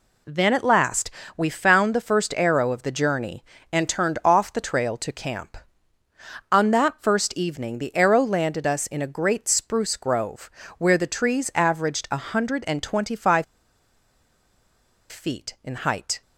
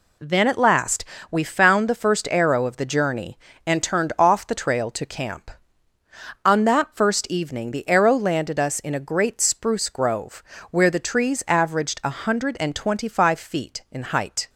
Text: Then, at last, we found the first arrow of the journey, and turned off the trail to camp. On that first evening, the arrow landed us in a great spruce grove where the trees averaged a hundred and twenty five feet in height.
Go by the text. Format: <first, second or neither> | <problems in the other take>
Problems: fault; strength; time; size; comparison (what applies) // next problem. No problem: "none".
second | pauses between "grove" and "where"; slight; at 10.4 s; 0.30 s long; slight in the second // pauses between "five" and "feet"; strong; at 13.4 s; 1.6 s long